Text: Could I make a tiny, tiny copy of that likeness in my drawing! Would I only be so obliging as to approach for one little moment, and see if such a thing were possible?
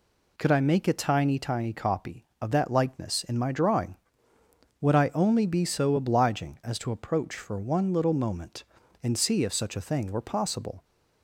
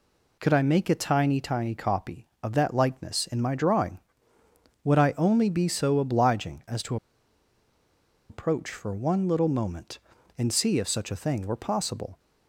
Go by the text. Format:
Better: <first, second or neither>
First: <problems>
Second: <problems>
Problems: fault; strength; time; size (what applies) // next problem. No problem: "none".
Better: first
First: none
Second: pauses between "to" and "approach"; strong; at 6.9 s; 1.3 s long